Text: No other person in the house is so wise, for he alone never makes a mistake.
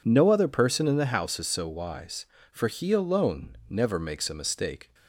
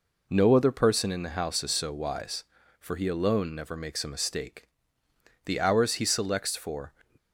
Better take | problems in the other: first | goes on to say "The hours he selects for"; from 5.4 s on; 1.4 s long

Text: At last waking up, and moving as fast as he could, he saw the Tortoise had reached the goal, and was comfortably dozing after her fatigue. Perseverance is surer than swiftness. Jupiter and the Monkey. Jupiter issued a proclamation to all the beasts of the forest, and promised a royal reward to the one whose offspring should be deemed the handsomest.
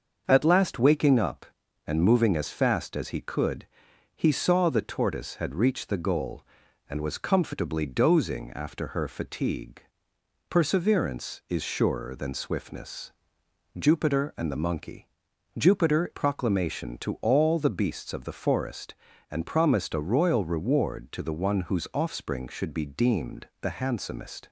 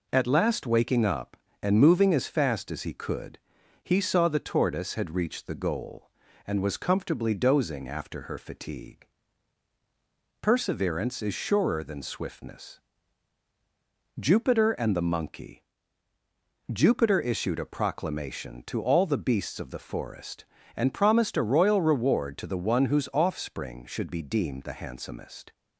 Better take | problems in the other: second | starts louder than the rest; until 1.2 s; 6.5 dB // skips "issued a"; at 16.1 s

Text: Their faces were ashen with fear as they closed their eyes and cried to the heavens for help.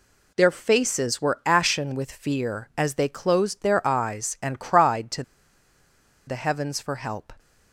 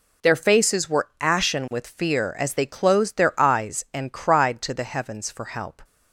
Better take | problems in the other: second | pauses between "to" and "the"; at 5.2 s; 1.0 s long

